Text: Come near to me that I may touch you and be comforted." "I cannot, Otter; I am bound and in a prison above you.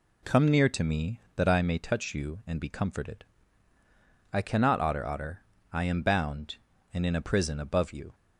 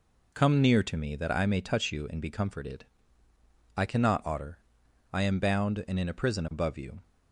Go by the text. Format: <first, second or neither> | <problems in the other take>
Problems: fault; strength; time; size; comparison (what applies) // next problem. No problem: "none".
second | says "Otter" twice; at 5.0 s